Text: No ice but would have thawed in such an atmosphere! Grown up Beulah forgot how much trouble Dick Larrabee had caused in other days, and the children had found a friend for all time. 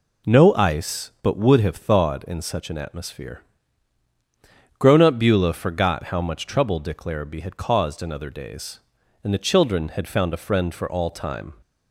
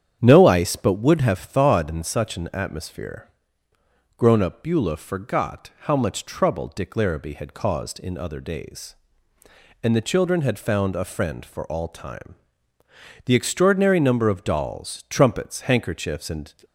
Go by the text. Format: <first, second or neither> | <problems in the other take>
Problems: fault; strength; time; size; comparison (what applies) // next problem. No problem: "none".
first | starts louder than the rest; strong; until 1.2 s; 9 dB // goes on to say "The extraordinary number of dolls trumpets handkerchiefs and"; strong; from 13.2 s on; 3.2 s long